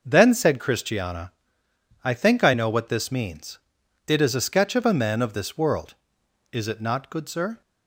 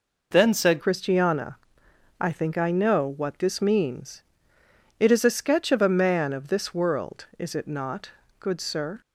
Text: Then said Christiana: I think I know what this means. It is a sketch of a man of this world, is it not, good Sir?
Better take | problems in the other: first | changes voice at "Christiana"; from 0.7 s on; 8.3 s long

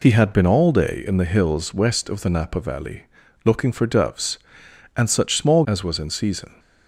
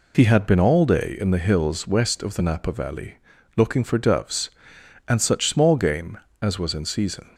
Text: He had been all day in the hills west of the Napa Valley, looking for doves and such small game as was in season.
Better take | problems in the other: second | skips "game"; at 5.6 s

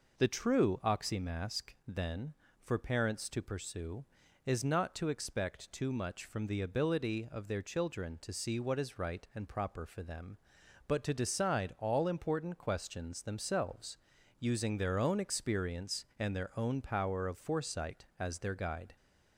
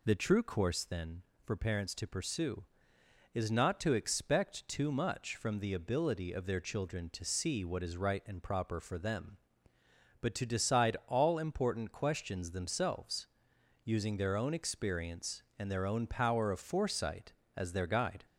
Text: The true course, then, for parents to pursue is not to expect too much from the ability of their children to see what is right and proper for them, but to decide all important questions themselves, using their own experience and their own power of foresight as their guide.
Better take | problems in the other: second | says "oxymask" for "course"; at 0.8 s

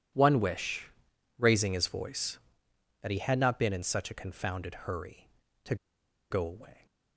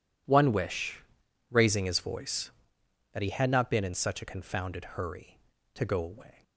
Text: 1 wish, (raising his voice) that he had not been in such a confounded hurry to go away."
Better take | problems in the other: second | pauses between "to" and "go"; noticeable; at 5.7 s; 0.55 s long

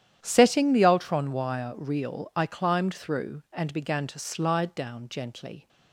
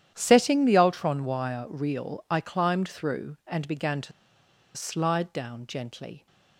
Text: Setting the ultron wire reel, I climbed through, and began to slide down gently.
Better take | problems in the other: first | starts louder than the rest; strong; until 1.1 s; 10.5 dB; strong in the first // pauses between "to" and "slide"; noticeable; at 4.1 s; 0.64 s long

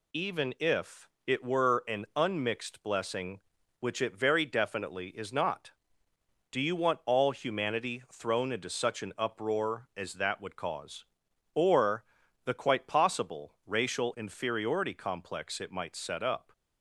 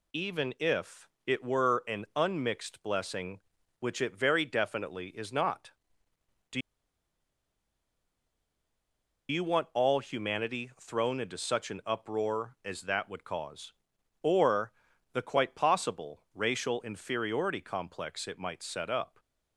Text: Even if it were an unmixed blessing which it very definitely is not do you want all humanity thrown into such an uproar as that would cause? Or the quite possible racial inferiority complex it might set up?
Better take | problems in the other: first | pauses between "if" and "it"; slight; at 1.0 s; 0.16 s long; slight in the first // pauses between "do" and "you"; strong; at 6.6 s; 2.6 s long // pauses between "Or" and "the"; at 14.7 s; 0.40 s long; also in the first

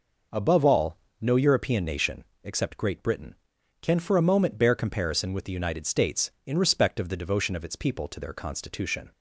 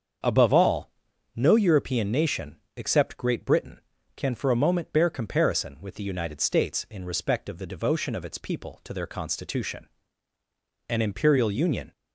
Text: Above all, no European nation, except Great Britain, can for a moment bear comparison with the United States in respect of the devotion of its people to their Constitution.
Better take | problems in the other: first | starts louder than the rest; until 1.6 s; 7 dB // goes on to say "An imperial union"; noticeable; from 10.8 s on; 1.0 s long

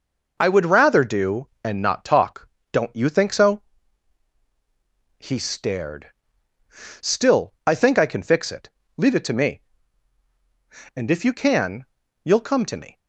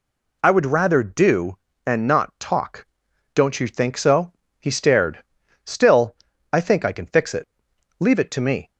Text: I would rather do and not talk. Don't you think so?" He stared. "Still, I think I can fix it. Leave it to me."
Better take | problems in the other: second | goes on to say "And if you can you'll come to me"; strong; from 10.9 s on; 2.0 s long

